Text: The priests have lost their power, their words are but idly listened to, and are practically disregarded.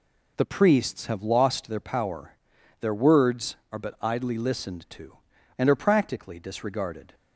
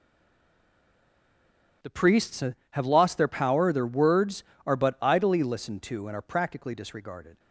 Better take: first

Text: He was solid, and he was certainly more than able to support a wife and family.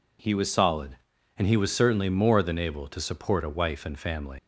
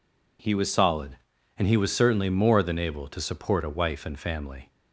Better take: second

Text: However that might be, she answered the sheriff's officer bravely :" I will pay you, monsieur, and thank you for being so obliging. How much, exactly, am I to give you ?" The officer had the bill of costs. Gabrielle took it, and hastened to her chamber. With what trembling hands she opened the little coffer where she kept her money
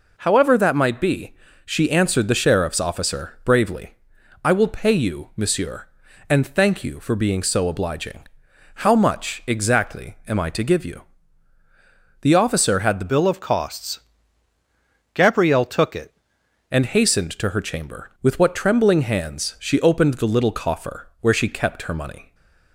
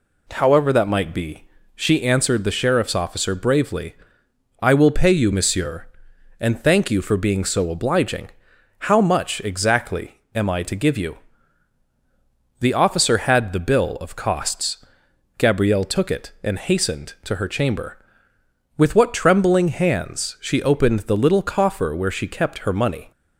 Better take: second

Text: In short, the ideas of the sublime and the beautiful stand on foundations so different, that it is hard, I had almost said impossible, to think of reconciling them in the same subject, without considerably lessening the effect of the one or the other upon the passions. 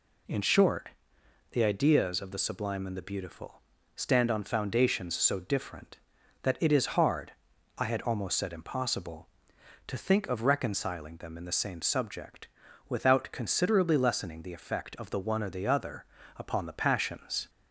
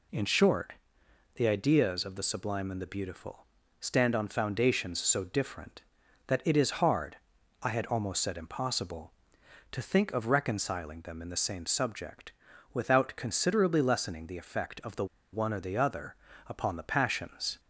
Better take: first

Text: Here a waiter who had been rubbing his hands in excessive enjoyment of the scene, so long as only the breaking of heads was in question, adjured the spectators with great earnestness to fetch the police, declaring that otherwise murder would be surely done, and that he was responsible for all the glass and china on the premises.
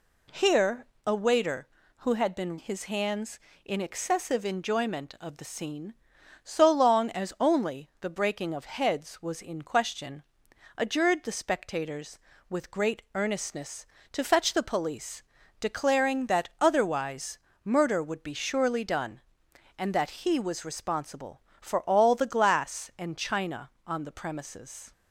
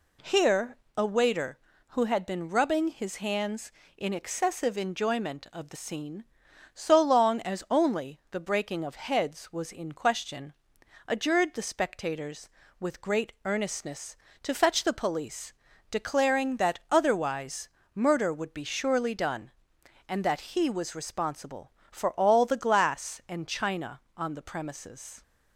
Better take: second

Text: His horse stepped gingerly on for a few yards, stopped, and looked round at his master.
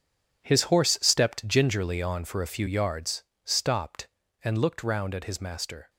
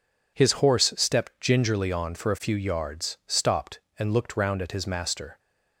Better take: second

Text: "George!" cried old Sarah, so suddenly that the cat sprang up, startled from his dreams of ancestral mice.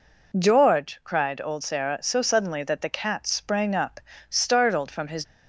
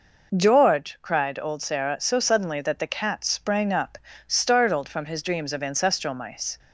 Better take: second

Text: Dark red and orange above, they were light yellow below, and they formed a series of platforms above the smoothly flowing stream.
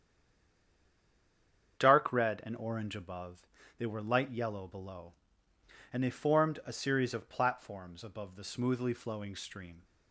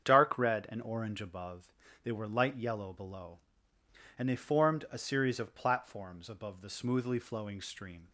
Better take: second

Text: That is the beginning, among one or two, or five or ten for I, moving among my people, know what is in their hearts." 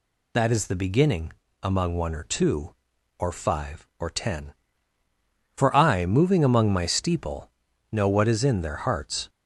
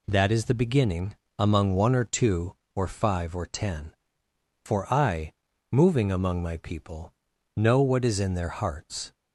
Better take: second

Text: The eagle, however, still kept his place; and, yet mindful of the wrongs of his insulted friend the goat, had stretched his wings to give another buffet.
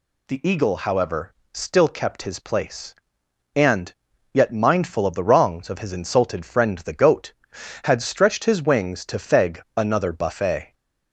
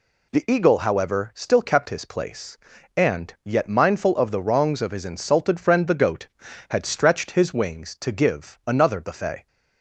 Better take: second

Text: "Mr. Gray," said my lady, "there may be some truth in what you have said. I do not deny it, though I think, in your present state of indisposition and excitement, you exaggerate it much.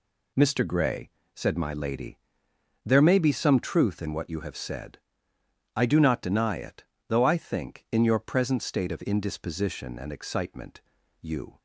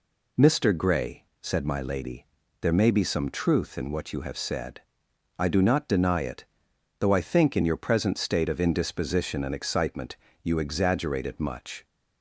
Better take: second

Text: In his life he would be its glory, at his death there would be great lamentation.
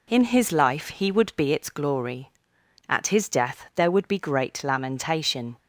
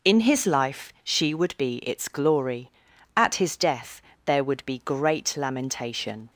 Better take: first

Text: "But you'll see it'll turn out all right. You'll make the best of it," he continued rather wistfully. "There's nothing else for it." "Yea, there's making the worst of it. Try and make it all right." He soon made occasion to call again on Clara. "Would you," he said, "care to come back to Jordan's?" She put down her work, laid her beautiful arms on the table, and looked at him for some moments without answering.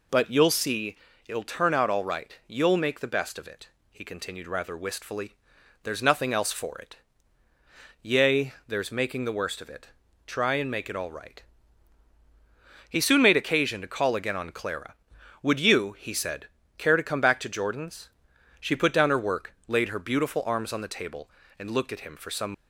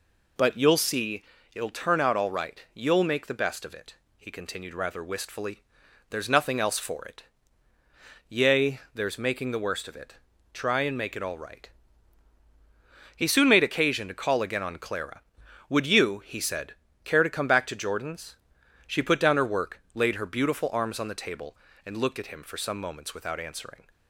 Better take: second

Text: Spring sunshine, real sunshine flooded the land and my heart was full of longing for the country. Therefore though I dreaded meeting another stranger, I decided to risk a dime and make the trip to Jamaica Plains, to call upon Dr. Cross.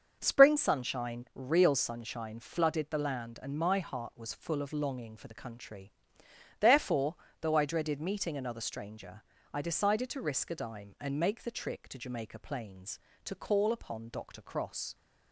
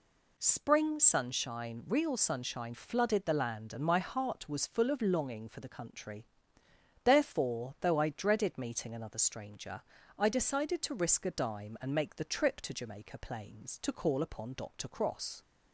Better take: second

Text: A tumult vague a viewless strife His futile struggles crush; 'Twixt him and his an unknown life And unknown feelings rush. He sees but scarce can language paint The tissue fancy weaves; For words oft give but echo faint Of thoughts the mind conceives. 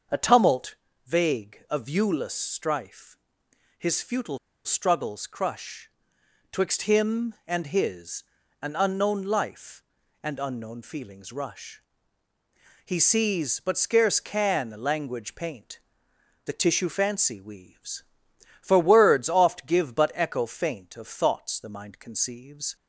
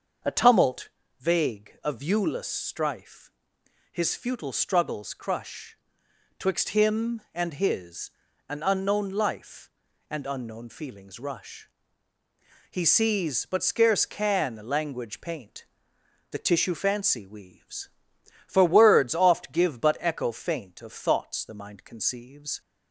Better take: second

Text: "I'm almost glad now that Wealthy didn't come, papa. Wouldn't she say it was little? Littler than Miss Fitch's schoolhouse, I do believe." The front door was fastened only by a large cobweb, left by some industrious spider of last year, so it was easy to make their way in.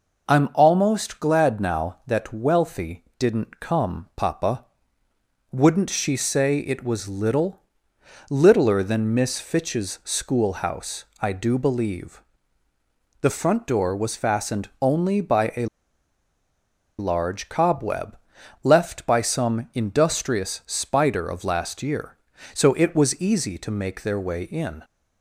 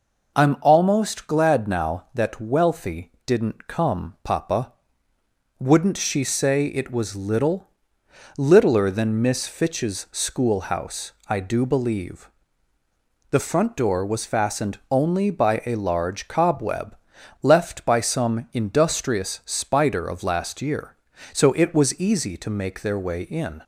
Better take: second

